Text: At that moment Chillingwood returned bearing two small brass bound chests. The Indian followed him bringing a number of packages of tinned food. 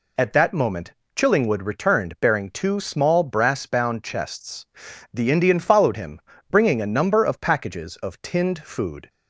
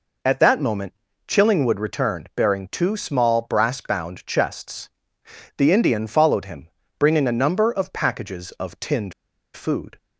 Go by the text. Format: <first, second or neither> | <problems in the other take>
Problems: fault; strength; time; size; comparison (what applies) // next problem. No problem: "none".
first | pauses between "moment" and "Chillingwood"; slight; at 0.9 s; 0.34 s long; slight in the first // pauses between "him" and "bringing"; slight; at 6.6 s; 0.30 s long; slight in the first // pauses between "tinned" and "food"; at 9.1 s; 0.42 s long